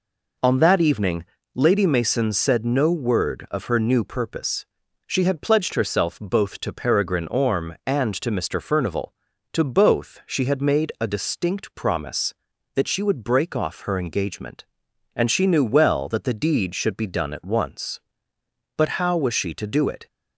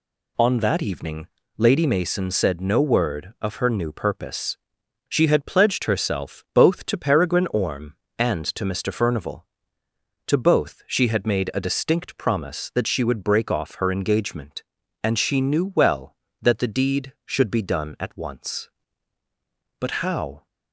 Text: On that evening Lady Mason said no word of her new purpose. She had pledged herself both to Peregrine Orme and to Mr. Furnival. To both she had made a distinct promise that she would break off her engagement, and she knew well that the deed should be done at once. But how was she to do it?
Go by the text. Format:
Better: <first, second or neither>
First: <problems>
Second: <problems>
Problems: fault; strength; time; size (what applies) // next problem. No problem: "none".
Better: first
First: pauses between "evening" and "Lady"; slight; at 1.2 s; 0.32 s long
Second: pauses between "evening" and "Lady"; slight; at 1.2 s; 0.30 s long // stops before "was she to do it"; at 20.4 s